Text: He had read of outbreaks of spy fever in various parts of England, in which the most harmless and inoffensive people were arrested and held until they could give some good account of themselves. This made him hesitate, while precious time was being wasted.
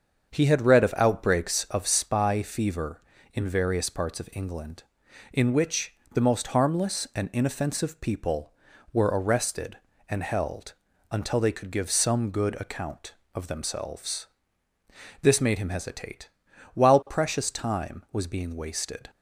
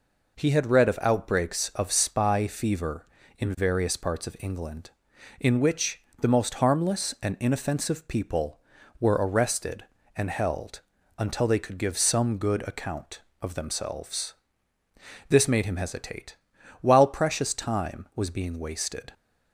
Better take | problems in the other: second | starts louder than the rest; until 1.8 s; 7 dB // pauses between "which" and "the"; slight; at 5.9 s; 0.18 s long; slight in the second // pauses between "held" and "until"; slight; at 10.7 s; 0.36 s long; slight in the second

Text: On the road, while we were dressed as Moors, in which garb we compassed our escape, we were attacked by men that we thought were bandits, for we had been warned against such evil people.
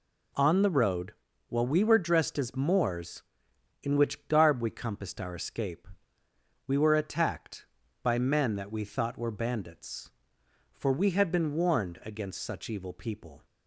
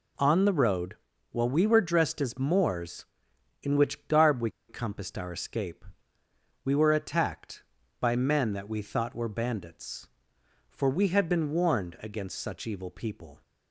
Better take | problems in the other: first | pauses between "we" and "compassed"; slight; at 4.4 s; 0.19 s long

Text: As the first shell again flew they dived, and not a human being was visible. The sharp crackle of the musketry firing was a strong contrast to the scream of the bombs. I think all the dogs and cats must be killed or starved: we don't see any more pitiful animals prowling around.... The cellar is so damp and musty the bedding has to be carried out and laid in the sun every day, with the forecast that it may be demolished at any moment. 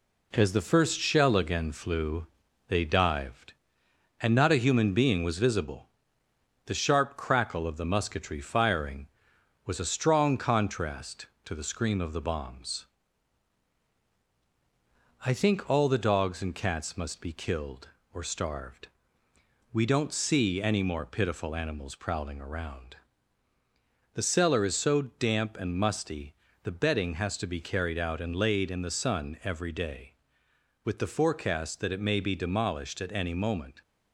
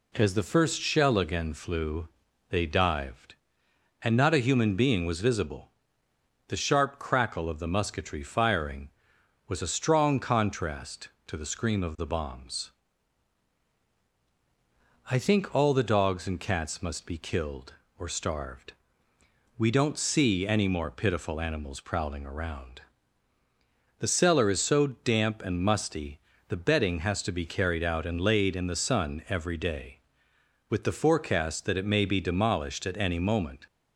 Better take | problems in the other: second | gets quieter; noticeable; throughout; 4 dB // pauses between "flew" and "they"; at 2.2 s; 0.44 s long; also in the second // pauses between "musty" and "the"; slight; at 26.3 s; 0.30 s long; slight in the second

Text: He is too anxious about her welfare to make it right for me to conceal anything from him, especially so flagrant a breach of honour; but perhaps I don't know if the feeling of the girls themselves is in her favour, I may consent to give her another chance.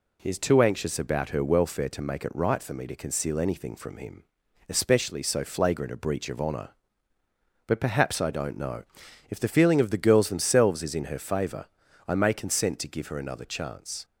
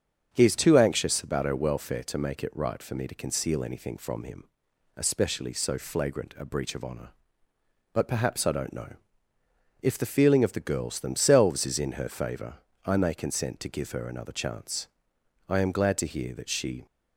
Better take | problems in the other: first | starts louder than the rest; strong; until 1.3 s; 7 dB // pauses between "know" and "if"; noticeable; at 8.9 s; 0.88 s long; noticeable in the first // goes on to say "I am glad to hear that she"; from 15.4 s on; 1.3 s long

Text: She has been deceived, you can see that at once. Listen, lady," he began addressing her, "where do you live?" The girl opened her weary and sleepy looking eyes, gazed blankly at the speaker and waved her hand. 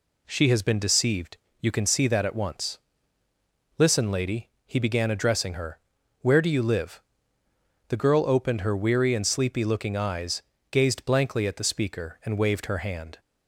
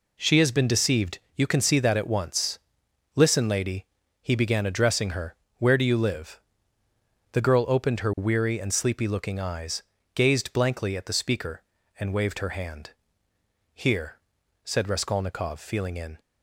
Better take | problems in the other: first | goes on to say "Here said Raskolnikov feeling in"; strong; from 13.7 s on; 2.4 s long

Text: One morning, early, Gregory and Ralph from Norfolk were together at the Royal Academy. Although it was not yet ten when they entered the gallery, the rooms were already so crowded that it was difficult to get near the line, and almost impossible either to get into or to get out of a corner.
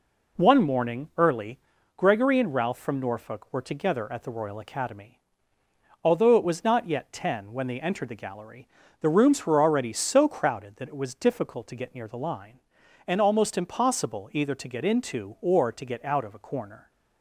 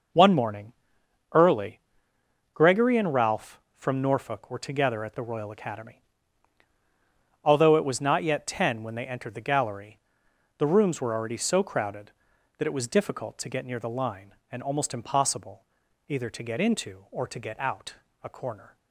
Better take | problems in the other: first | pauses between "impossible" and "either"; at 15.6 s; 0.42 s long // skips "of"; at 18.0 s

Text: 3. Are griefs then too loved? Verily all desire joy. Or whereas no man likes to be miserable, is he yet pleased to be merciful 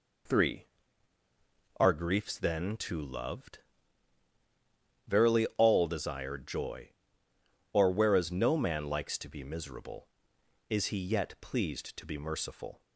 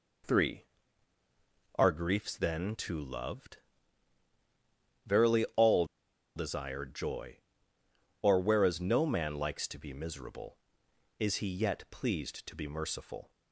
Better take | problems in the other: first | pauses between "all" and "desire"; noticeable; at 5.8 s; 0.51 s long

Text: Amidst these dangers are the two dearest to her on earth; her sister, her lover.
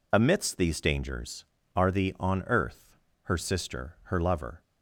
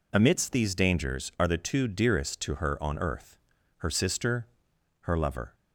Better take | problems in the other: second | skips "two dearest to her"; at 2.1 s

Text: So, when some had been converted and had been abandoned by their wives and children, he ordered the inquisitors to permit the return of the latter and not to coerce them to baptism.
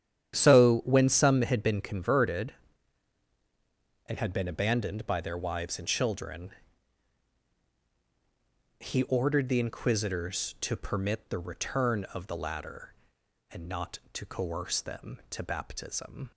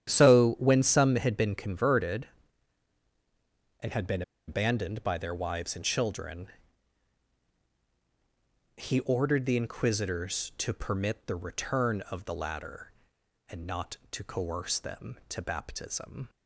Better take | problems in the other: first | starts louder than the rest; strong; until 1.1 s; 10 dB; strong in the first // pauses between "been" and "abandoned"; slight; at 4.2 s; 0.25 s long

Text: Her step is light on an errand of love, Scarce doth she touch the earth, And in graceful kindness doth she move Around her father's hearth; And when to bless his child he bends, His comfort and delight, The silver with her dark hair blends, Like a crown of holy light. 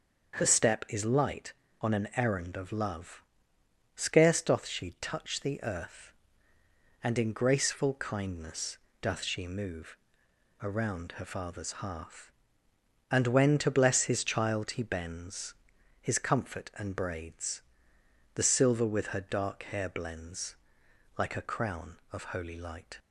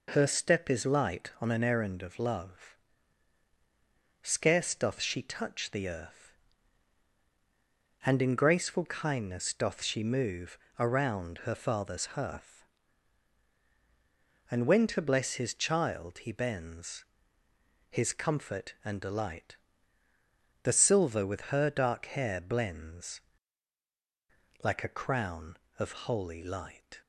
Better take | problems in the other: second | starts louder than the rest; until 1.4 s; 6.5 dB // pauses between "kindness" and "doth"; slight; at 8.7 s; 0.22 s long // pauses between "move" and "Around"; noticeable; at 9.9 s; 0.64 s long; slight in the second // says "braids" for "delight"; at 16.9 s

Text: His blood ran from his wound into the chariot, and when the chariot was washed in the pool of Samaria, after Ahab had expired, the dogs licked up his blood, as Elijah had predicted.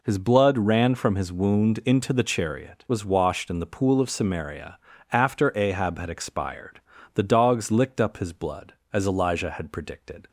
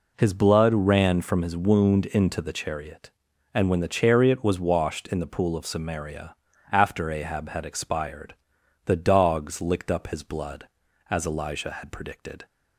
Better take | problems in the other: second | skips "and when the chariot"; at 2.8 s

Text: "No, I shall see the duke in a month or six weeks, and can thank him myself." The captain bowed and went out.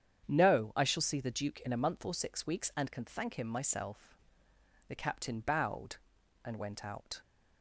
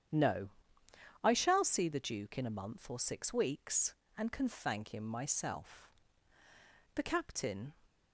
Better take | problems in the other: first | starts louder than the rest; strong; until 1.8 s; 9 dB; strong in the first // stops before "bowed and went out"; at 7.8 s

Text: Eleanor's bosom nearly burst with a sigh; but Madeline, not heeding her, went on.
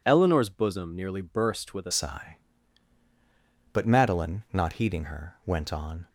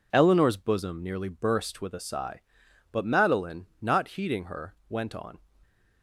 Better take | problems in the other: second | changes voice at "sigh"; from 1.9 s on; 4.1 s long

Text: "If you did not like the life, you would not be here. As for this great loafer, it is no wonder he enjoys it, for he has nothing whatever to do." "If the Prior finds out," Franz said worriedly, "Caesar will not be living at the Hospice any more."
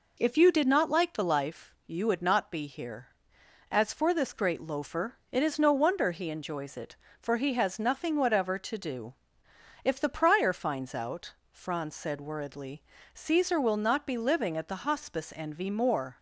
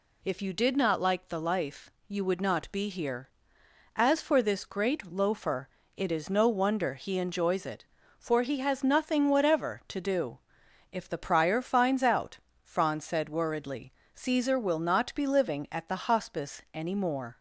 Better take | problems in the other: second | says "envy" for "any"; at 15.3 s

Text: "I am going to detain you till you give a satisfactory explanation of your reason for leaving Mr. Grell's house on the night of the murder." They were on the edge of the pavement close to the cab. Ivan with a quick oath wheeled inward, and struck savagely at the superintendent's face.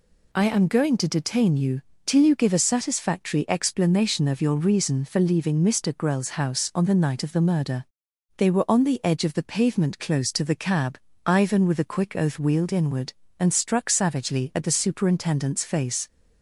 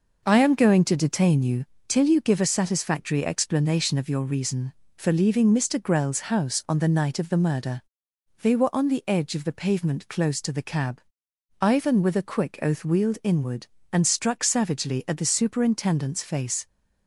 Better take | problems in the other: first | starts louder than the rest; noticeable; until 1.7 s; 5.5 dB // pauses between "you" and "till"; slight; at 1.6 s; 0.22 s long; slight in the first

